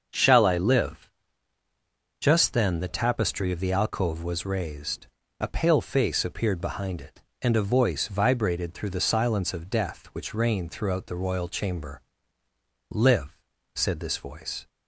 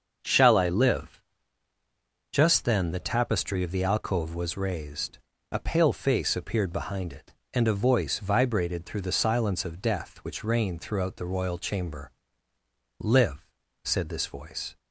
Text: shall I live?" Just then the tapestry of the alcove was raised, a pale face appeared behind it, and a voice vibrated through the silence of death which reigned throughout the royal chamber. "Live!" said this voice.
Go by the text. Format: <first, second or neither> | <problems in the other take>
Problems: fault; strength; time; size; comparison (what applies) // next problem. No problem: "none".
neither | starts louder than the rest; the same in both